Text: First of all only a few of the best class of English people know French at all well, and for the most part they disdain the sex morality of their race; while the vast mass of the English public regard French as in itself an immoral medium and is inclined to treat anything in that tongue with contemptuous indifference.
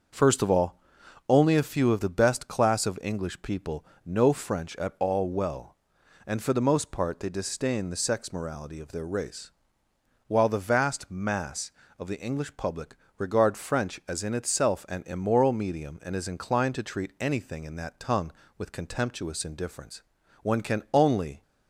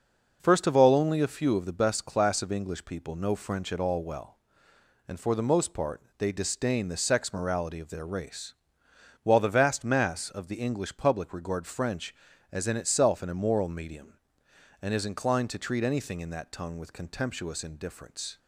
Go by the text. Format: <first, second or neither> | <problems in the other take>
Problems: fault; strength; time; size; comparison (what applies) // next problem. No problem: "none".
second | starts louder than the rest; until 1.6 s; 6.5 dB // pauses between "all" and "only"; noticeable; at 0.7 s; 0.48 s long // pauses between "people" and "know"; slight; at 3.8 s; 0.22 s long // pauses between "public" and "regard"; slight; at 12.9 s; 0.22 s long // goes on to say "One can only"; noticeable; from 20.4 s on; 0.98 s long